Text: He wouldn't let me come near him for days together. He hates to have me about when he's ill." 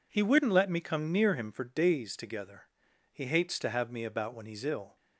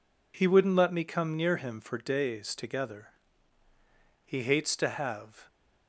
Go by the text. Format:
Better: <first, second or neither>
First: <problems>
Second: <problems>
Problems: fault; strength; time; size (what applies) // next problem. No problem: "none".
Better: first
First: none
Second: stops before "me about when he's ill"; at 5.4 s